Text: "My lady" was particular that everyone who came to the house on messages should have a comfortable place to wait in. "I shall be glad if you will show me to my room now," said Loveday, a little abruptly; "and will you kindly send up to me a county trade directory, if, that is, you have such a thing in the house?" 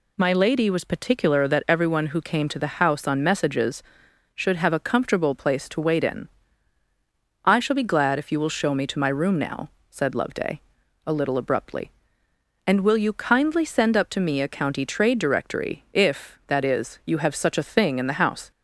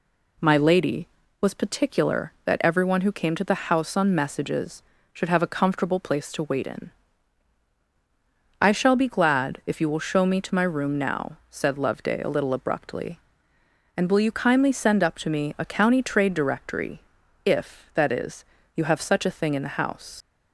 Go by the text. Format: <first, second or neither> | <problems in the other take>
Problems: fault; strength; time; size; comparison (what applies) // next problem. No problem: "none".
first | leaves "house" unfinished; at 20.2 s; 155 ms